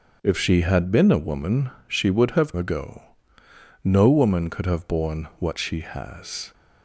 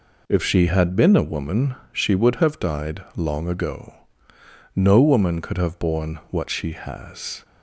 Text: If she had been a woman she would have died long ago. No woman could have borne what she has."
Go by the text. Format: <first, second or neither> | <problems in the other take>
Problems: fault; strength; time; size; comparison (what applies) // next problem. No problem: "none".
second | starts louder than the rest; until 1.2 s; 7 dB // pauses between "woman" and "she"; slight; at 1.6 s; 0.18 s long; slight in the second // skips "died long"; at 2.5 s